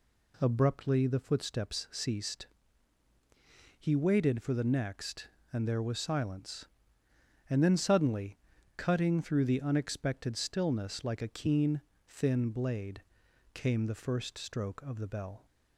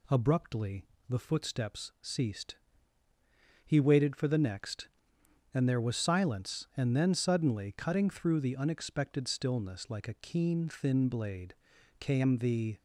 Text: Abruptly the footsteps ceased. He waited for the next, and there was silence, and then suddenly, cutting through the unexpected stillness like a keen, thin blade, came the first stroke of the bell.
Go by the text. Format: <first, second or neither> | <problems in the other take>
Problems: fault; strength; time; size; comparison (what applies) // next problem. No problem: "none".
first | pauses between "Abruptly" and "the"; slight; at 0.8 s; 0.24 s long // stops before "first stroke of the bell"; at 12.7 s